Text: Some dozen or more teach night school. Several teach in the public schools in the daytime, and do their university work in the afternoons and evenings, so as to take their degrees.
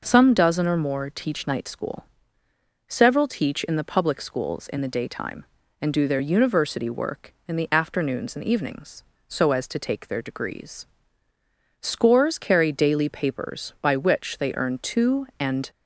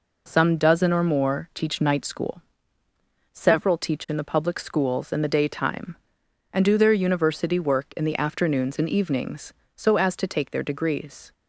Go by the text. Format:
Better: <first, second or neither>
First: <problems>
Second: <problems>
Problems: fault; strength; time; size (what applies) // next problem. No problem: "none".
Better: second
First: goes on to say "Scores carry daily papers by which they earn two and"; strong; from 11.8 s on; 3.8 s long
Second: none